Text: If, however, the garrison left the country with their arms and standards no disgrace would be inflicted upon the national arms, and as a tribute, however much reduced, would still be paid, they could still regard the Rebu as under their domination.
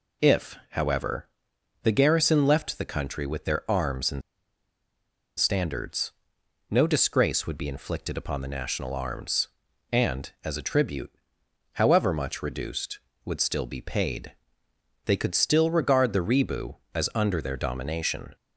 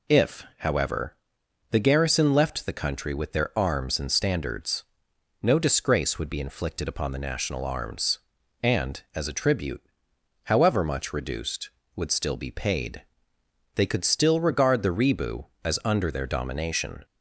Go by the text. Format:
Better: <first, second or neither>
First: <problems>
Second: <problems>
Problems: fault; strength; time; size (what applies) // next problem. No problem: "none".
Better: second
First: pauses between "and" and "standards"; at 4.2 s; 1.1 s long // pauses between "standards" and "no"; noticeable; at 6.1 s; 0.58 s long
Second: pauses between "standards" and "no"; noticeable; at 4.8 s; 0.58 s long